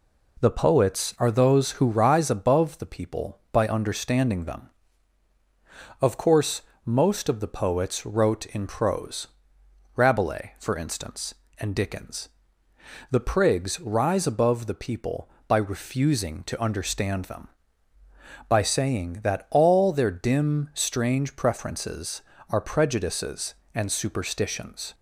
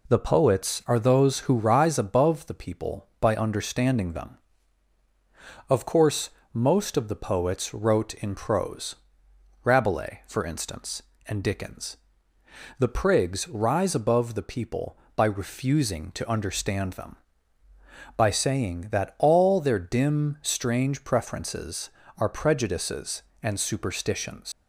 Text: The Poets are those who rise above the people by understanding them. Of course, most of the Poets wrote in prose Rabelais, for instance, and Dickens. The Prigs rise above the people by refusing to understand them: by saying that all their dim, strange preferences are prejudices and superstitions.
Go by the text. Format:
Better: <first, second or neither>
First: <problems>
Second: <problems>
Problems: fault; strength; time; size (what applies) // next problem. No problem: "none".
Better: first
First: pauses between "prose" and "Rabelais"; noticeable; at 9.2 s; 0.70 s long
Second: pauses between "prose" and "Rabelais"; noticeable; at 8.9 s; 0.70 s long // leaves "superstitions" unfinished; at 24.5 s; 100 ms